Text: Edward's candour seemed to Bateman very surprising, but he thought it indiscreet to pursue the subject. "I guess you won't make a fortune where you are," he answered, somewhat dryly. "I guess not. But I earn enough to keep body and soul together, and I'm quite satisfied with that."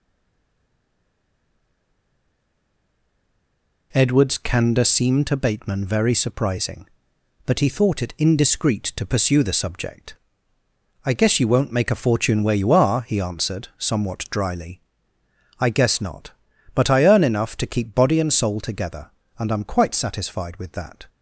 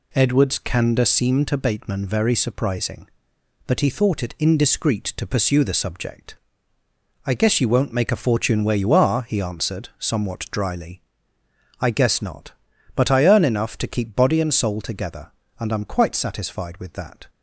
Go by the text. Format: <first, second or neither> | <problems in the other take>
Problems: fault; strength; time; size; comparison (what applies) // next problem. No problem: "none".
second | stays silent before the first word; strong; until 3.9 s; 3.9 s long